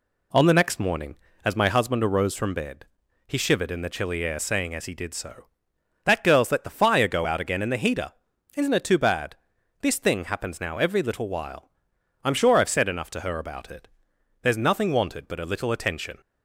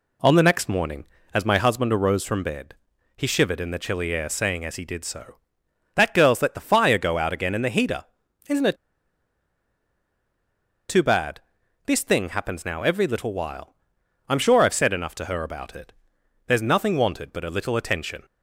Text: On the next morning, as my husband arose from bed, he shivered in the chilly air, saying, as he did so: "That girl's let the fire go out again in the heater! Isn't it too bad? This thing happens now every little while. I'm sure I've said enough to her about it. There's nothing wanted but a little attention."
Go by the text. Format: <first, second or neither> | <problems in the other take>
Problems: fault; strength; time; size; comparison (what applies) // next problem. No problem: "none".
first | pauses between "it" and "too"; strong; at 8.7 s; 2.1 s long